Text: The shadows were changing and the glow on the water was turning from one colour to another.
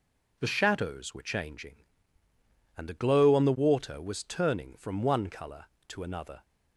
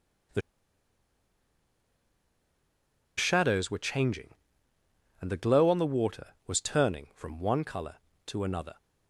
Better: first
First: none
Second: pauses between "The" and "shadows"; strong; at 0.4 s; 2.7 s long

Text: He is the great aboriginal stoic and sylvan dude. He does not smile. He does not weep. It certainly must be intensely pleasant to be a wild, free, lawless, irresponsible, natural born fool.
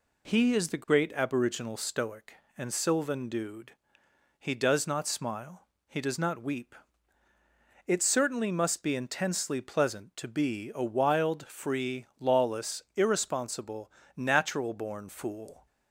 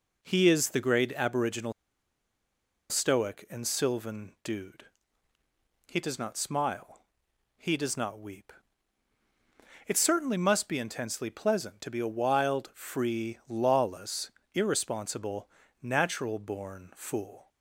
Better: first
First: none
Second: pauses between "aboriginal" and "stoic"; at 1.7 s; 1.1 s long

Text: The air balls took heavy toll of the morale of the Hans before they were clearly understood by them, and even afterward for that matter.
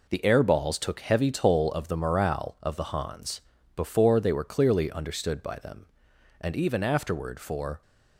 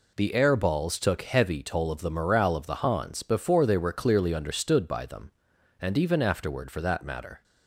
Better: second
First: pauses between "Hans" and "before"; slight; at 3.4 s; 0.34 s long // stops before "that matter"; at 7.8 s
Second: none

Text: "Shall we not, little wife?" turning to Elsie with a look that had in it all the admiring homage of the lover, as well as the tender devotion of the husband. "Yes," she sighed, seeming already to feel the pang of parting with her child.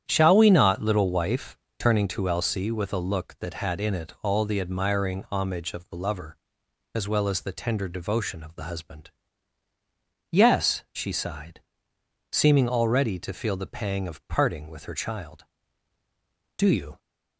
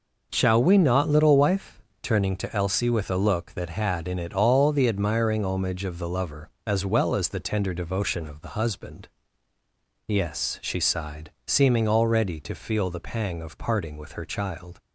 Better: second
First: starts louder than the rest; strong; until 1.0 s; 10 dB // goes on to say "Do you"; slight; from 16.5 s on; 0.42 s long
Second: none

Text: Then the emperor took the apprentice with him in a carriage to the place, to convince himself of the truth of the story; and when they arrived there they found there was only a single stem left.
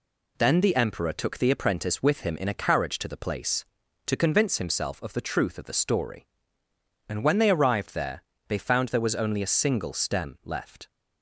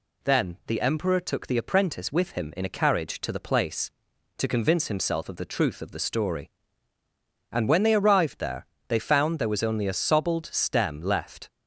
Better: first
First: pauses between "there" and "they"; slight; at 8.2 s; 0.28 s long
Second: pauses between "there" and "they"; slight; at 8.6 s; 0.24 s long // says "sobbled" for "single"; at 9.9 s

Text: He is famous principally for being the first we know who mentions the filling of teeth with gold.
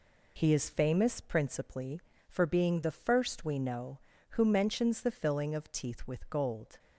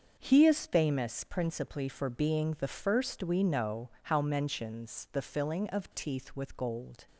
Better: first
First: none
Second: starts louder than the rest; until 1.2 s; 6.5 dB // says "how" for "who"; at 4.0 s

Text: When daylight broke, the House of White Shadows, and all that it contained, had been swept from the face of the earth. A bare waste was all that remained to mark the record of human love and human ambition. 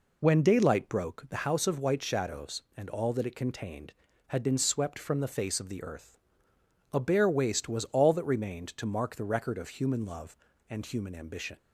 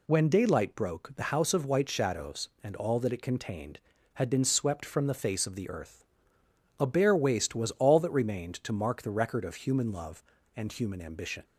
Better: second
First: starts louder than the rest; until 1.2 s; 3.5 dB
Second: none

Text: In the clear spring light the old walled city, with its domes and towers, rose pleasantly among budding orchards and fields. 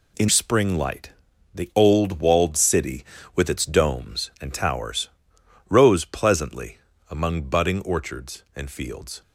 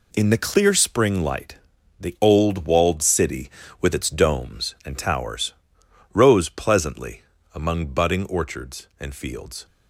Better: second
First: skips "the clear"; at 0.2 s // pauses between "light" and "the"; at 1.0 s; 0.42 s long // pauses between "pleasantly" and "among"; slight; at 6.7 s; 0.32 s long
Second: pauses between "light" and "the"; at 1.5 s; 0.42 s long // pauses between "pleasantly" and "among"; slight; at 7.2 s; 0.32 s long

